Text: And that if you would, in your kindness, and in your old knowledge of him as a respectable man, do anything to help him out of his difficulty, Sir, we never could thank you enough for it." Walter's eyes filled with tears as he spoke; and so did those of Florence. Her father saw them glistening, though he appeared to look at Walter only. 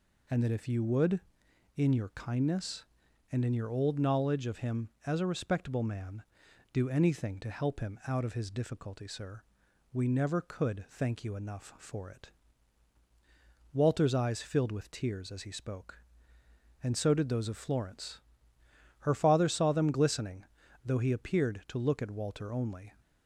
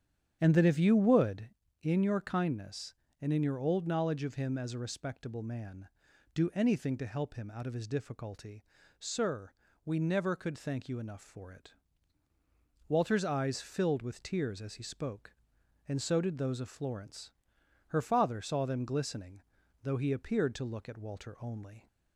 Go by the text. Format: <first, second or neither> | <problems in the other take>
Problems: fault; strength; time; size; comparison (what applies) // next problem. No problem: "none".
first | starts louder than the rest; strong; until 1.8 s; 9 dB